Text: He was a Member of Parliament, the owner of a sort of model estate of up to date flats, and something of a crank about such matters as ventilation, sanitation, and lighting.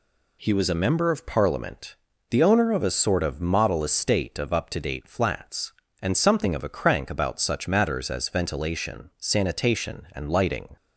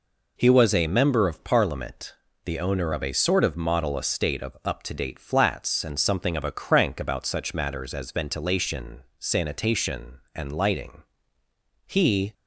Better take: first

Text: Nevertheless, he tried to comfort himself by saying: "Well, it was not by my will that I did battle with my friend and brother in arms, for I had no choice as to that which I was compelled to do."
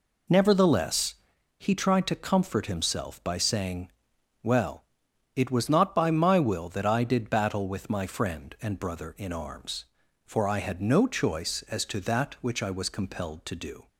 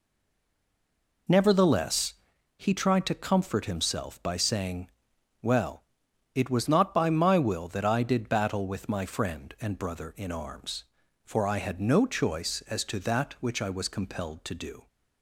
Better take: first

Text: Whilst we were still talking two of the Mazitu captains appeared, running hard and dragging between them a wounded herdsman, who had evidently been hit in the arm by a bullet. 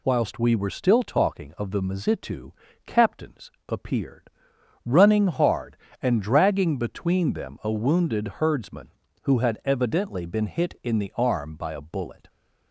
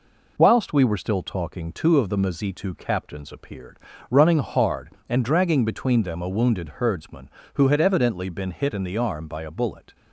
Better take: second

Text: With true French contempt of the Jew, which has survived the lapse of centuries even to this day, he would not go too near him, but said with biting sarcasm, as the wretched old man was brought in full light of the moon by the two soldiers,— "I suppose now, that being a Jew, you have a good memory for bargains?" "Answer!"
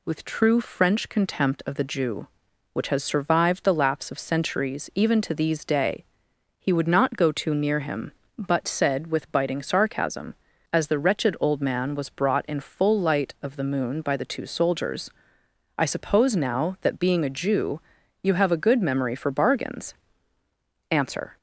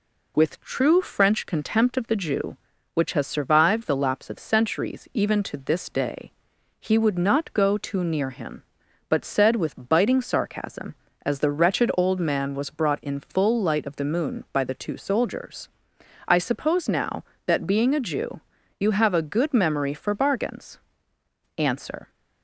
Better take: second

